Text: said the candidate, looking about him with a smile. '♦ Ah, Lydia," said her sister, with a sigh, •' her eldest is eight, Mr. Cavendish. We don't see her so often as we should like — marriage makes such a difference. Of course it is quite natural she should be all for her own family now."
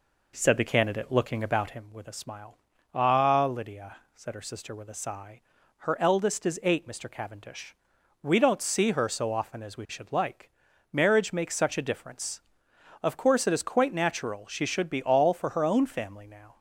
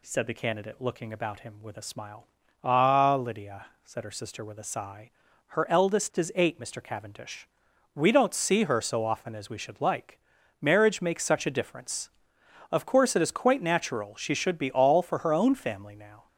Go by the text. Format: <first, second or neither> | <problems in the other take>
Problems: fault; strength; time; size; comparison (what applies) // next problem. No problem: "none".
second | starts louder than the rest; until 1.8 s; 3.5 dB